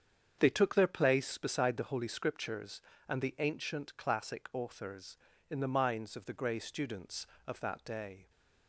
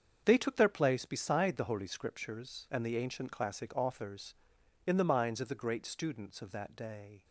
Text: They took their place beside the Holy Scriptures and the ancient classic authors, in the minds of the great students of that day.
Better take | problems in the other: second | starts louder than the rest; strong; until 1.4 s; 7.5 dB; also in the second // says "grey" for "great"; at 6.3 s

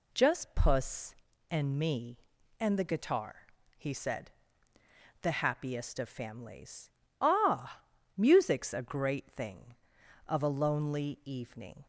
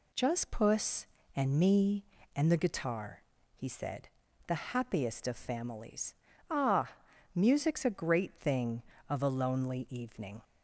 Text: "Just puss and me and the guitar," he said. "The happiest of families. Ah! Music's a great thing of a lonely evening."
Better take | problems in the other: neither | none

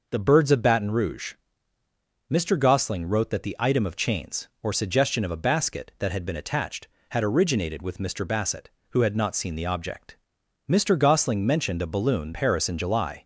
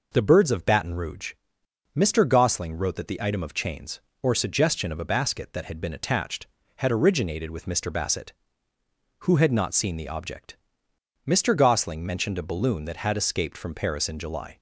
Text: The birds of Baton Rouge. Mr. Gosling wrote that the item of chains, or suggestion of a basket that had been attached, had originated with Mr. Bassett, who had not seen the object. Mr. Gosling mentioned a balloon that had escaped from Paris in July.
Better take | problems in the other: second | skips "that had escaped from"; at 12.3 s

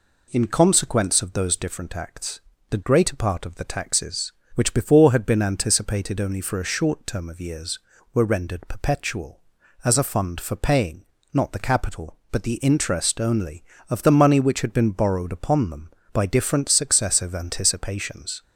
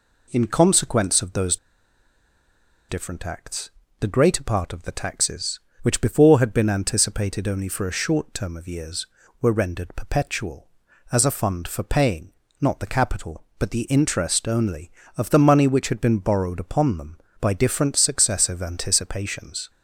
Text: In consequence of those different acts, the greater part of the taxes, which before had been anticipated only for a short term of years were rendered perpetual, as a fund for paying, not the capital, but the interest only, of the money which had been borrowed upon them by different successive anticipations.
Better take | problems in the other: first | pauses between "those" and "different"; strong; at 1.5 s; 1.3 s long

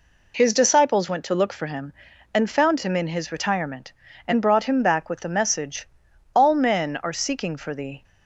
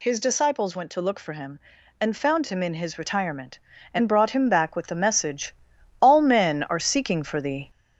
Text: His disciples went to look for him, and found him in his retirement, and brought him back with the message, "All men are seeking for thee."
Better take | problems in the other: first | gets louder; noticeable; throughout; 4 dB

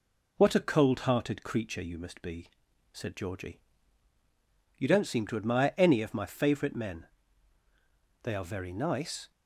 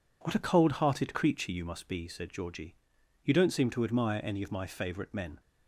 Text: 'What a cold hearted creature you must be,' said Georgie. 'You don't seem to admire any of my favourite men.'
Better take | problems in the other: second | goes on to say "They are very nice"; noticeable; from 8.2 s on; 1.0 s long

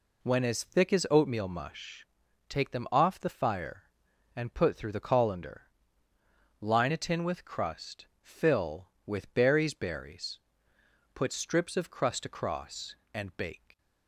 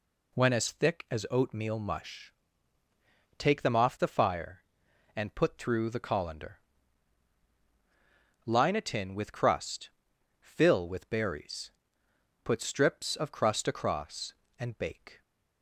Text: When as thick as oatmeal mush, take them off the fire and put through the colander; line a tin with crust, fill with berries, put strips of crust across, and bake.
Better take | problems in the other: second | says "berries" twice; at 9.7 s

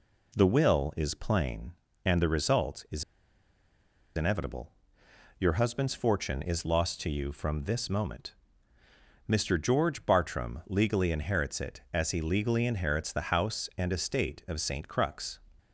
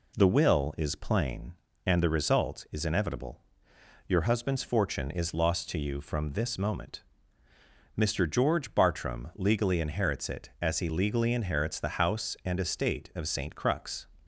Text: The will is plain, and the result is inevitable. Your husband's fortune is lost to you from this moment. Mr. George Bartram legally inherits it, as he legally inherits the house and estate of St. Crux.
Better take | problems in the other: second | pauses between "is" and "inevitable"; at 3.0 s; 1.1 s long

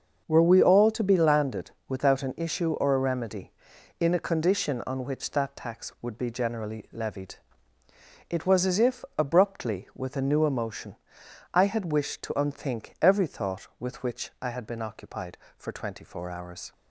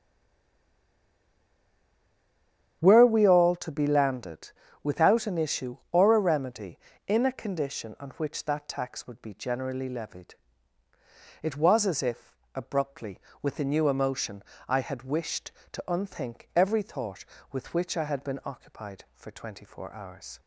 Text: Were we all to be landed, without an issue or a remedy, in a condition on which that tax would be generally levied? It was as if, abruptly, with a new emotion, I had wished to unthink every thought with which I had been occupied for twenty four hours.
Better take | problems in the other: first | stays silent before the first word; strong; until 2.8 s; 2.8 s long // starts louder than the rest; strong; until 3.8 s; 9 dB; also in the first

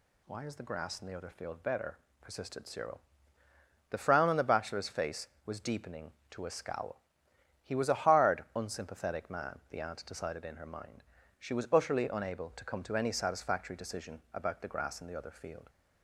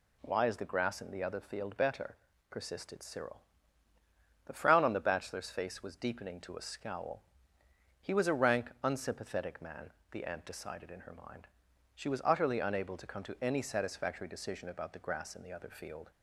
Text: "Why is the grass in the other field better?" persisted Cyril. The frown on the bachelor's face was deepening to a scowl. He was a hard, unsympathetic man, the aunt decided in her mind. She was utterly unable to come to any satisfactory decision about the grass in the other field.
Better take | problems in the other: first | says "rank" for "hard"; at 8.3 s

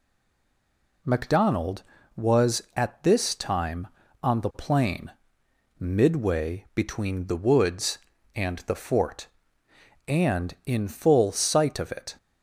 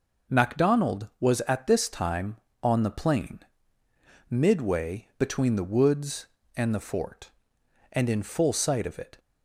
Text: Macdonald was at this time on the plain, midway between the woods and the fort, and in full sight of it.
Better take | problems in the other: second | stays silent before the first word; until 1.0 s; 1.0 s long

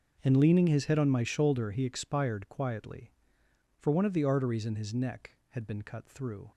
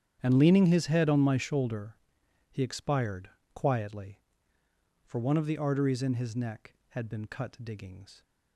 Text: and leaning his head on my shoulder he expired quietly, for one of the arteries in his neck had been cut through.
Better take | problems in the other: first | starts louder than the rest; strong; until 1.2 s; 9 dB; also in the first // pauses between "shoulder" and "he"; noticeable; at 1.9 s; 0.56 s long // pauses between "expired" and "quietly"; slight; at 3.2 s; 0.24 s long // says "diggings" for "through"; at 7.6 s

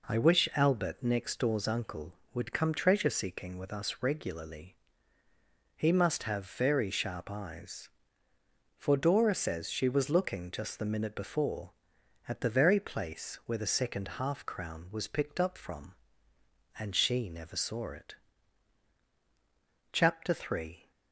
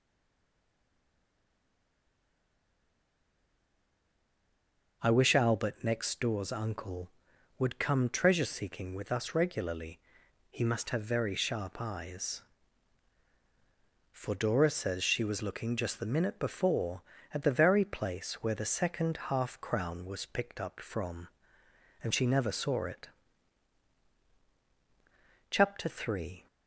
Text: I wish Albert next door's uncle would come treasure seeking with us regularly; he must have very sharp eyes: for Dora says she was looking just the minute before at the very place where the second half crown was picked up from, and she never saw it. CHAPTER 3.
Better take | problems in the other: first | stays silent before the first word; strong; until 5.0 s; 5.0 s long

